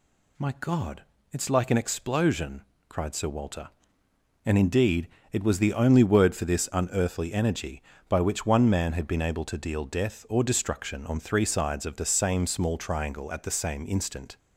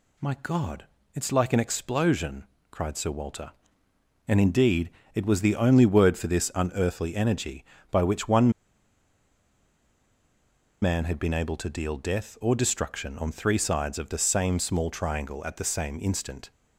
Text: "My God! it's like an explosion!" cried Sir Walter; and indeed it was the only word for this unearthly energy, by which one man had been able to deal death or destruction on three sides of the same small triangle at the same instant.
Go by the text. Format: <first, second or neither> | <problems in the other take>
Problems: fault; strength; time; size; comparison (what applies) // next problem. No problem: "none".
first | pauses between "indeed" and "it"; slight; at 4.8 s; 0.24 s long; slight in the first // pauses between "one" and "man"; strong; at 8.5 s; 2.3 s long